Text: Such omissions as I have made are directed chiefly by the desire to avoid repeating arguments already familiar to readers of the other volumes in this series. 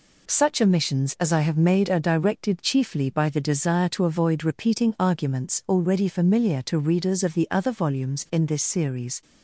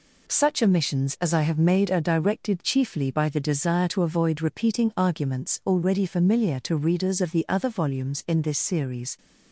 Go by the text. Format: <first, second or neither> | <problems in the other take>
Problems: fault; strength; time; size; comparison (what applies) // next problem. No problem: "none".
neither | none